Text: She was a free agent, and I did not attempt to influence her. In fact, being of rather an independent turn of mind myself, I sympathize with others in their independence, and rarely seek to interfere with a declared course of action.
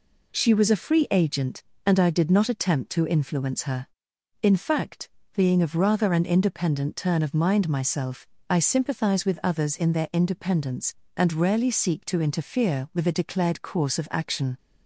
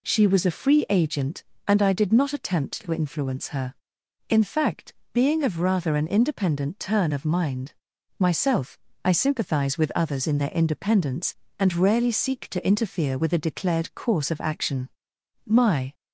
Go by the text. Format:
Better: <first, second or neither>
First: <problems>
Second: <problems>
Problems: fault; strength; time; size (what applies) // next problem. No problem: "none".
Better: first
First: none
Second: pauses between "mind" and "myself"; noticeable; at 7.7 s; 0.48 s long // goes on to say "My"; slight; from 15.4 s on; 0.48 s long